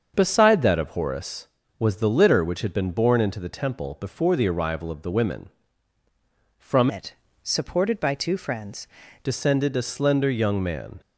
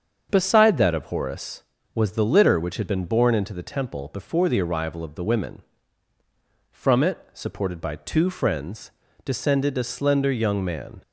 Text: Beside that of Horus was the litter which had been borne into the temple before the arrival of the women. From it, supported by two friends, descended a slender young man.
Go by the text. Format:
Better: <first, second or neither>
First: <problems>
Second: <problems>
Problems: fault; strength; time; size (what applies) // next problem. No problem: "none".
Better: second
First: starts louder than the rest; until 1.1 s; 7 dB // changes voice from "it" to "friends"; from 6.8 to 8.8 s; 2.0 s long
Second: starts louder than the rest; until 1.3 s; 7 dB